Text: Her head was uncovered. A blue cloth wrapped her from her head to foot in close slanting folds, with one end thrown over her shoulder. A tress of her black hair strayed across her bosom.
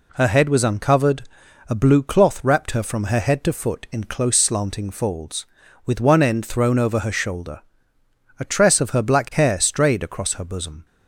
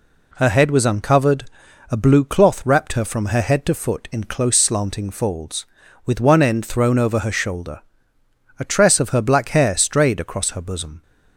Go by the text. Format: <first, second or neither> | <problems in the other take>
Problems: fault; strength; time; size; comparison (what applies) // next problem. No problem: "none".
neither | none